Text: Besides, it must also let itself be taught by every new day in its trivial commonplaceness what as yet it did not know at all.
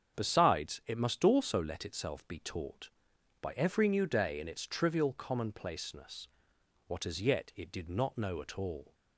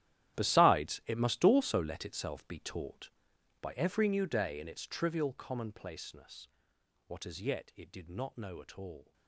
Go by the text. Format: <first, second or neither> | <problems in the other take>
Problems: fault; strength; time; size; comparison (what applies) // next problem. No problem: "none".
first | gets quieter; strong; throughout; 17 dB // starts louder than the rest; strong; until 1.4 s; 12.5 dB; strong in the first // pauses between "commonplaceness" and "what"; noticeable; at 6.4 s; 0.60 s long; noticeable in the first